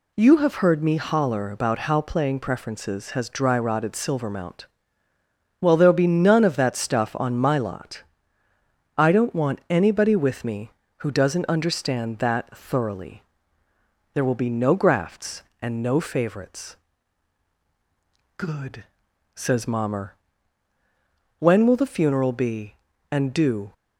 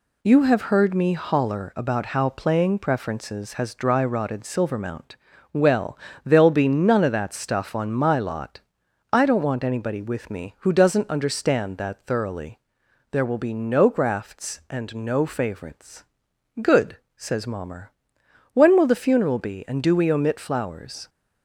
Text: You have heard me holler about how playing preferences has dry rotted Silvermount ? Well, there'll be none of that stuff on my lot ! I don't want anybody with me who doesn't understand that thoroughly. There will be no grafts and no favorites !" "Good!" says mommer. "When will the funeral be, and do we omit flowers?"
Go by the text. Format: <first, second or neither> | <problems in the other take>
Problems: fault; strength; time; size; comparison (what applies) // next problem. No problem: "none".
second | stops before "we omit flowers"; at 23.7 s